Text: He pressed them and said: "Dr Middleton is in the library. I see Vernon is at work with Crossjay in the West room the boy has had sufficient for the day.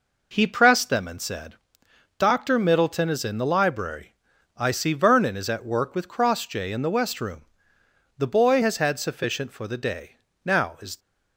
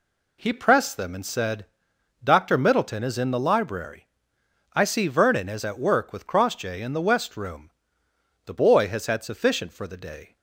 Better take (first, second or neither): second